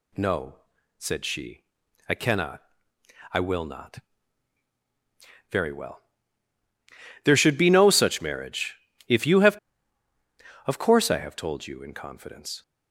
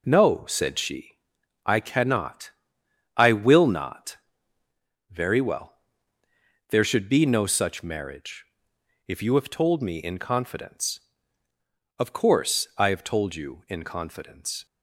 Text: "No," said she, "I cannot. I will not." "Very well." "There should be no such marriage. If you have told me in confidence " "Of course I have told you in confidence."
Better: second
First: skips "told me in confidence"; at 9.7 s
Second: none

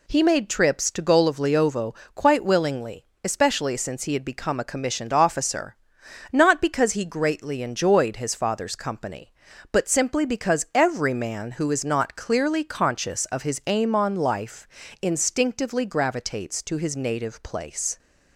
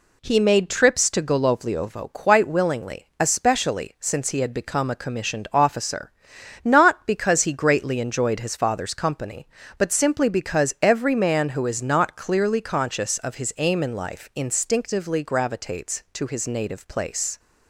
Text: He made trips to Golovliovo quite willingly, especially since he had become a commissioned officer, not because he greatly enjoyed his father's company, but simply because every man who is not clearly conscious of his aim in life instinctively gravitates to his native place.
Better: second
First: pauses between "Golovliovo" and "quite"; slight; at 1.9 s; 0.20 s long // says "on" for "in"; at 13.9 s // pauses between "life" and "instinctively"; slight; at 14.6 s; 0.34 s long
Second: none

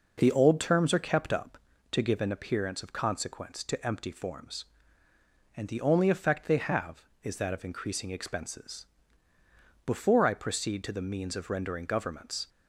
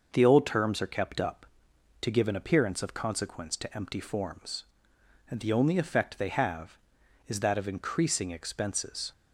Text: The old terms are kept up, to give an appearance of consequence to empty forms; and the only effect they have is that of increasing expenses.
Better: second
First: goes on to say "Before I proceed to the means of rendering governments"; strong; from 9.8 s on; 2.6 s long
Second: none

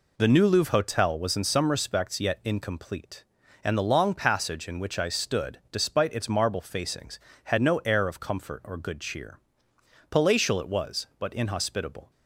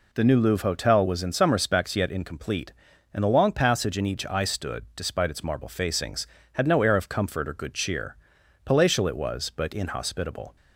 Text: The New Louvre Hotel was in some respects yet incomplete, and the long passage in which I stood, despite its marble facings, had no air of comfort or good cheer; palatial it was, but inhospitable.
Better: first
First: none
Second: says "each" for "which"; at 4.0 s

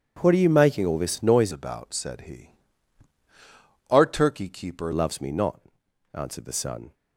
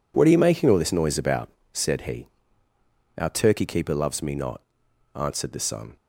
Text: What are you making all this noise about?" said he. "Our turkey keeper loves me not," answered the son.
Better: second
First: changes voice from "about" to "keeper"; from 1.5 to 4.9 s; 3.4 s long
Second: none

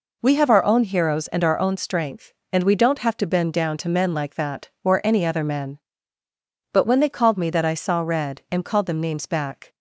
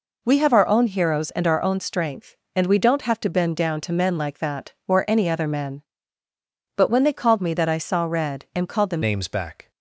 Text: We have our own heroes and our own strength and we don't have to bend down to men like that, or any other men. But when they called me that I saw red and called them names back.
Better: first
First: none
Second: changes voice at "names"; from 9.0 s on; 0.7 s long

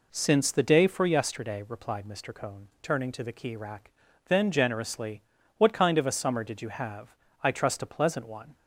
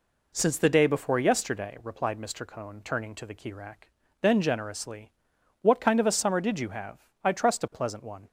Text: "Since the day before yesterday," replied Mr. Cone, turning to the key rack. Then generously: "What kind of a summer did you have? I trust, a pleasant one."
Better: second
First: says "for" for "before"; at 0.8 s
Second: none

